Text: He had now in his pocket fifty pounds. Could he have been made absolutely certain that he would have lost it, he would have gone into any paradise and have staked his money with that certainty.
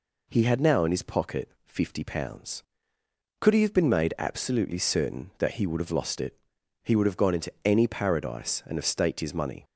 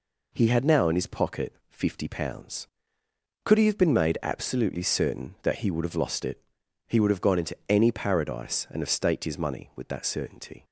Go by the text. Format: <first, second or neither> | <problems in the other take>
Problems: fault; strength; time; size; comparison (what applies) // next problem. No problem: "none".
second | pauses between "pocket" and "fifty"; slight; at 1.4 s; 0.18 s long; slight in the second // stops before "with that certainty"; at 9.6 s